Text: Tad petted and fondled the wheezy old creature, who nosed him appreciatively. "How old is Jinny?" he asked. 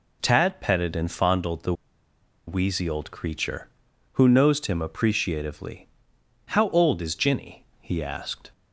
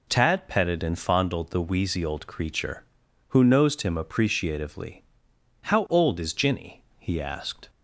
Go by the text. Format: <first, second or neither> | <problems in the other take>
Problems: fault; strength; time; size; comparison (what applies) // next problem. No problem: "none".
second | pauses between "the" and "wheezy"; noticeable; at 1.7 s; 0.74 s long